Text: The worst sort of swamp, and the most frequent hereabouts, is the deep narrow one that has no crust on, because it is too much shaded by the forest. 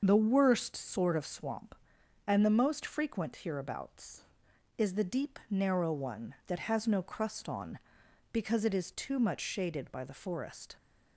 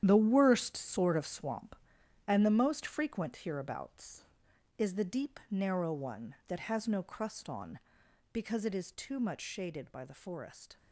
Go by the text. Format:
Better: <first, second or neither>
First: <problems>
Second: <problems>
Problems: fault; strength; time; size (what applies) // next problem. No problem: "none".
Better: first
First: starts louder than the rest; until 1.0 s; 6.5 dB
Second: gets quieter; strong; throughout; 11 dB // starts louder than the rest; strong; until 1.0 s; 10 dB